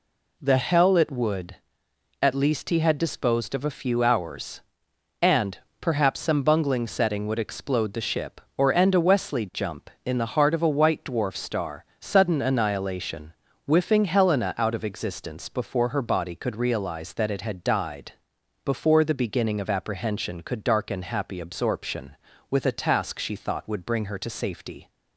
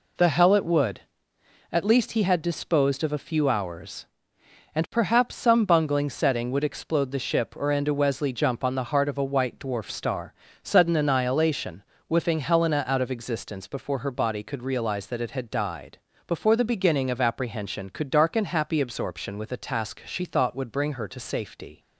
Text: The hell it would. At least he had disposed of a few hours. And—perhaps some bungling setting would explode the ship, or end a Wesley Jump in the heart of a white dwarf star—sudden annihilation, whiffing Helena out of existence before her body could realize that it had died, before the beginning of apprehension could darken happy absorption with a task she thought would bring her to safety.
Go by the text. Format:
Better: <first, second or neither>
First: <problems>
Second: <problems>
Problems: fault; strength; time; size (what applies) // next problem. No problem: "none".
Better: first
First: none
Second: says "on" for "in"; at 8.6 s